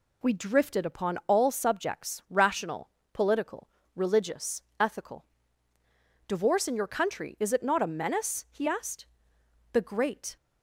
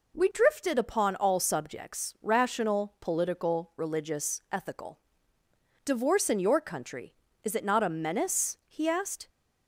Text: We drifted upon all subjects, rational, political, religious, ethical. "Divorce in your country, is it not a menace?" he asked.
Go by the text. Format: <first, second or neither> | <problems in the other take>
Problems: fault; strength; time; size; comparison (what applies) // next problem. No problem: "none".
second | goes on to say "The great"; noticeable; from 9.7 s on; 0.64 s long